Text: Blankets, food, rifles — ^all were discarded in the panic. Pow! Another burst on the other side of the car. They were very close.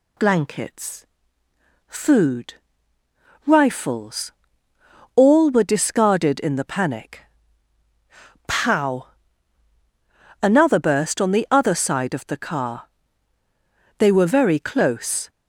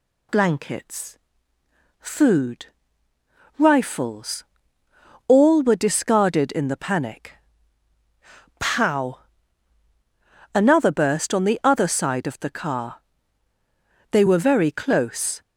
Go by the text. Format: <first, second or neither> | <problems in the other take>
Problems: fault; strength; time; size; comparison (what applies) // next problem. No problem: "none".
neither | none